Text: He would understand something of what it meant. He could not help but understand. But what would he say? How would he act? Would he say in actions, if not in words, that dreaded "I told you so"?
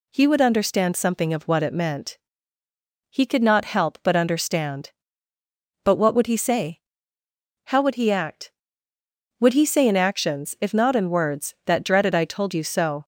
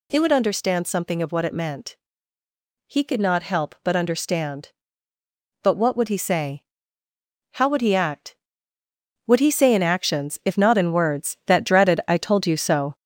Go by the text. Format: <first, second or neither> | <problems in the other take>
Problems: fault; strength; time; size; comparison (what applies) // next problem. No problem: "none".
first | gets louder; noticeable; throughout; 5 dB